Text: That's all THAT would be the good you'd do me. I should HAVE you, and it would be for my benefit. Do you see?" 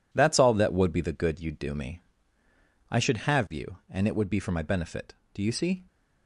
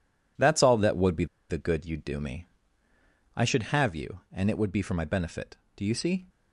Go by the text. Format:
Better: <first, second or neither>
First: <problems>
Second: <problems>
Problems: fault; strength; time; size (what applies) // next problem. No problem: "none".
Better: first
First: none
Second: pauses between "be" and "the"; slight; at 1.2 s; 0.24 s long